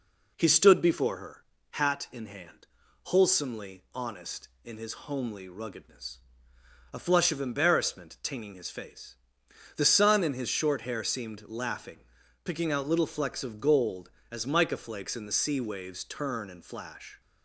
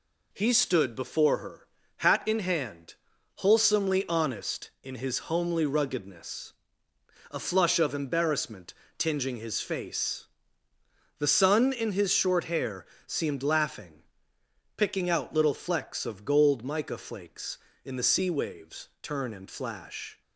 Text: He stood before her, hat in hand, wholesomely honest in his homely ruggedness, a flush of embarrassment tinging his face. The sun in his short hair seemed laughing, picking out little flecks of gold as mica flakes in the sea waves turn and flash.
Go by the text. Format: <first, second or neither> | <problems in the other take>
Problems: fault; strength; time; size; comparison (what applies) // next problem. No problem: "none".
first | pauses between "embarrassment" and "tinging"; slight; at 8.7 s; 0.24 s long // pauses between "hair" and "seemed"; slight; at 12.8 s; 0.22 s long // skips "as"; at 16.6 s